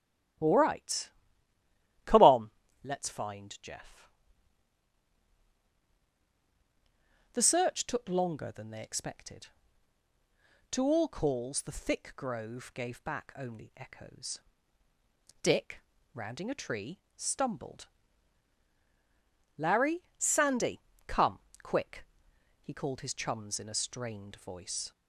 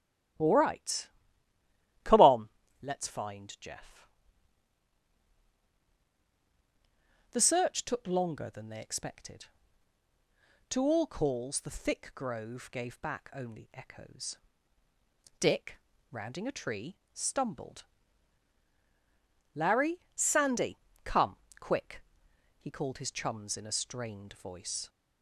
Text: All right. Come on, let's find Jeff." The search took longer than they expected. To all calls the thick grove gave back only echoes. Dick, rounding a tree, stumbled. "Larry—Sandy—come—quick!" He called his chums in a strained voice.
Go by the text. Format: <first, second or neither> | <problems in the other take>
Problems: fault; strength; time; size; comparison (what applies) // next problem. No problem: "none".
neither | starts louder than the rest; strong; the same in both